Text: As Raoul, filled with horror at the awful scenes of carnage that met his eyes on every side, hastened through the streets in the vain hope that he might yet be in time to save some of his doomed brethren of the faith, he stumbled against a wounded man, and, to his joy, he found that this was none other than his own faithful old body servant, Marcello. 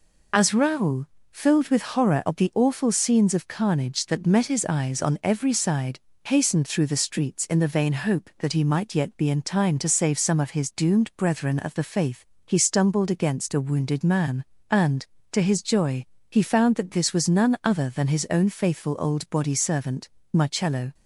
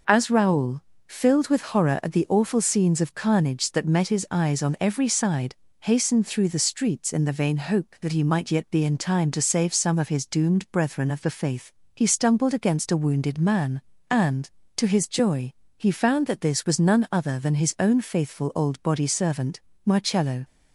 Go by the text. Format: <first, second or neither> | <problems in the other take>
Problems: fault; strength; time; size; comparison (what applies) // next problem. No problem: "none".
second | loses the start of "As"; at 0.3 s; 30 ms